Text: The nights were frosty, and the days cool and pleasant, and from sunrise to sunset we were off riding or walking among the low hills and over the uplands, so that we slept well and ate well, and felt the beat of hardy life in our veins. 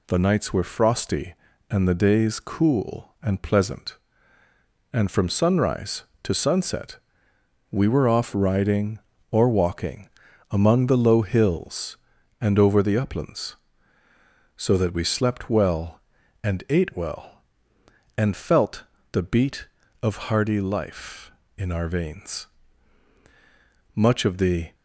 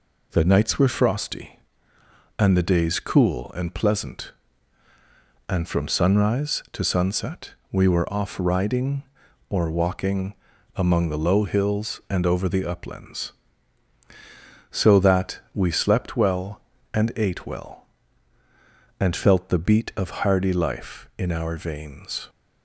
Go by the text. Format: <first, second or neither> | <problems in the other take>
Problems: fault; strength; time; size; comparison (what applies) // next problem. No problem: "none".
second | pauses between "sunset" and "we"; noticeable; at 6.9 s; 0.72 s long; slight in the second // pauses between "walking" and "among"; at 10.0 s; 0.42 s long; also in the second // pauses between "felt" and "the"; slight; at 18.8 s; 0.28 s long // goes on to say "Much of the"; noticeable; from 23.9 s on; 0.80 s long